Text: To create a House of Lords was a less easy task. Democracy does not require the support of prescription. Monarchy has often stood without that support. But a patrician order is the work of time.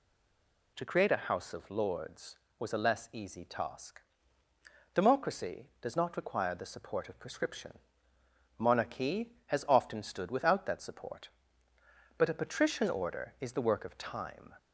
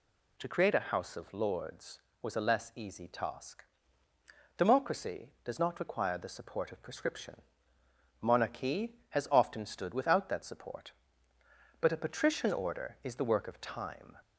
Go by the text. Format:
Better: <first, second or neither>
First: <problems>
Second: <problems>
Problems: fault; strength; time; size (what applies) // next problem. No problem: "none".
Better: second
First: stays silent before the first word; slight; until 0.7 s; 0.7 s long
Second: none